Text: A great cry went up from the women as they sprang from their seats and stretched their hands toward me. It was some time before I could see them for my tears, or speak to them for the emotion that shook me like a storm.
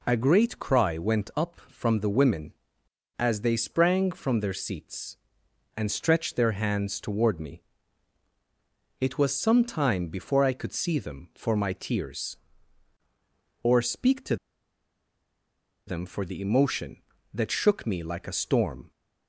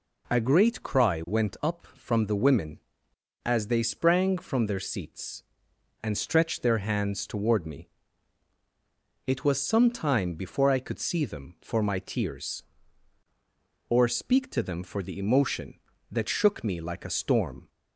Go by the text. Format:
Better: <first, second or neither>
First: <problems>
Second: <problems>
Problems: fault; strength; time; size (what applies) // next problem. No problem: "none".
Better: second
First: pauses between "to" and "them"; strong; at 14.3 s; 1.5 s long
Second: none